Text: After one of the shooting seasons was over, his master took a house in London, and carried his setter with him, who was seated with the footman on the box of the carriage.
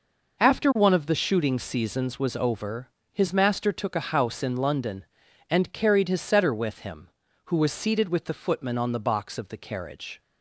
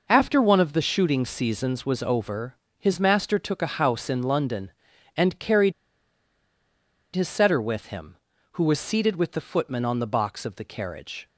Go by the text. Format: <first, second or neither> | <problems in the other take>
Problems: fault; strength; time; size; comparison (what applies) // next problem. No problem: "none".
first | pauses between "carried" and "his"; strong; at 5.7 s; 1.4 s long